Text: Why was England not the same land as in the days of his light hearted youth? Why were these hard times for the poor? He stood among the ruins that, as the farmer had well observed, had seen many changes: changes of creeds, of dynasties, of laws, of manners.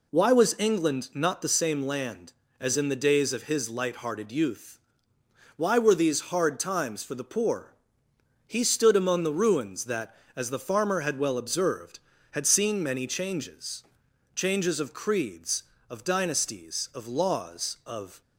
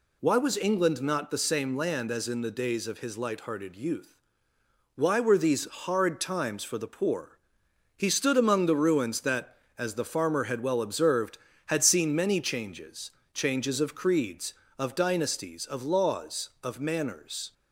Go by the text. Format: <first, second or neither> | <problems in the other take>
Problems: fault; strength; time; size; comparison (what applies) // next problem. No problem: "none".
second | stops before "manners"; at 18.2 s